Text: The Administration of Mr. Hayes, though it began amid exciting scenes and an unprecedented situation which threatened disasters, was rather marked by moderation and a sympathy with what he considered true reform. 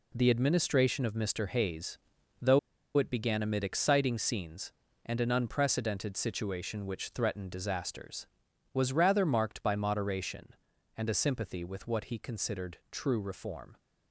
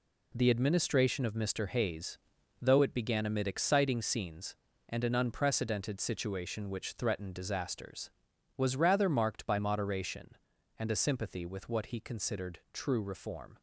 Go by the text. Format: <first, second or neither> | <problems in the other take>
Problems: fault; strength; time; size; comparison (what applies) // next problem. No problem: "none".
second | pauses between "though" and "it"; at 2.5 s; 0.37 s long